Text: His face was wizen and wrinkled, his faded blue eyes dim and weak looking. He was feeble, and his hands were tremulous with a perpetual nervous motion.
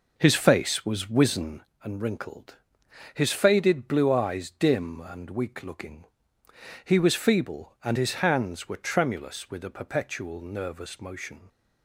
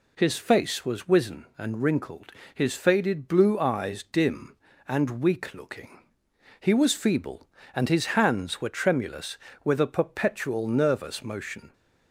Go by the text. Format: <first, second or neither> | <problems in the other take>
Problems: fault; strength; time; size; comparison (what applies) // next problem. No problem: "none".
second | starts louder than the rest; noticeable; until 1.6 s; 5 dB